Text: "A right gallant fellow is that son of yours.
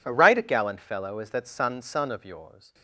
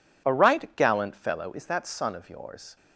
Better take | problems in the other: second | says "son" twice; at 1.7 s

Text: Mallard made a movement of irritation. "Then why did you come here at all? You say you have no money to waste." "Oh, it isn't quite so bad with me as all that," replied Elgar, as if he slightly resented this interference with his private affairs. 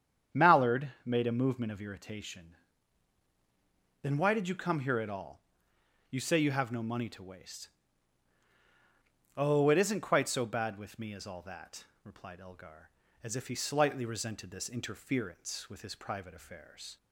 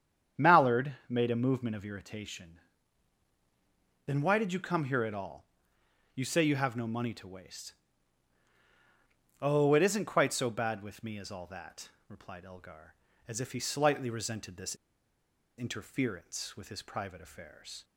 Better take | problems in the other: first | starts louder than the rest; strong; until 1.5 s; 8.5 dB; strong in the first // pauses between "this" and "interference"; noticeable; at 14.7 s; 0.82 s long

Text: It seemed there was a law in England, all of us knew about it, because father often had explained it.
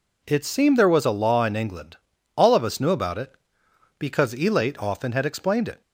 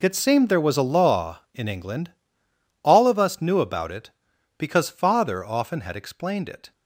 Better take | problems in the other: second | says "elate" for "father"; at 4.3 s

